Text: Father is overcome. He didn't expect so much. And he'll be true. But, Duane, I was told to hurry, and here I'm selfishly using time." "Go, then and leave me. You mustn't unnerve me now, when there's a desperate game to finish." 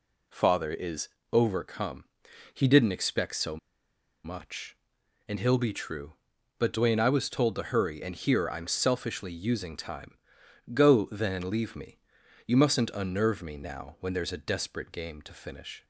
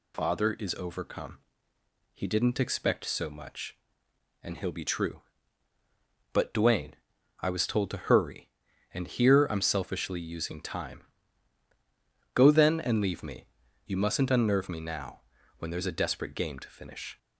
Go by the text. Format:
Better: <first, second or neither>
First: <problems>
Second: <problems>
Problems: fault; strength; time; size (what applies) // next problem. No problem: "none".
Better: second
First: pauses between "is" and "overcome"; slight; at 1.0 s; 0.24 s long // pauses between "so" and "much"; noticeable; at 3.5 s; 0.66 s long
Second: none